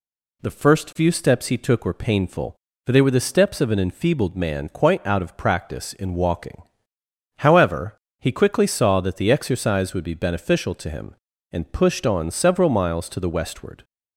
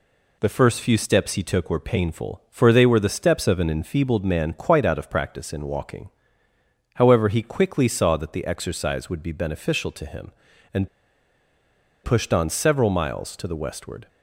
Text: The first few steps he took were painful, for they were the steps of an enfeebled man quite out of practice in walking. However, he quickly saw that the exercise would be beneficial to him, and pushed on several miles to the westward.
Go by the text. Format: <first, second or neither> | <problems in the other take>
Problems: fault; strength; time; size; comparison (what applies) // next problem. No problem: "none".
first | pauses between "and" and "pushed"; at 10.8 s; 1.1 s long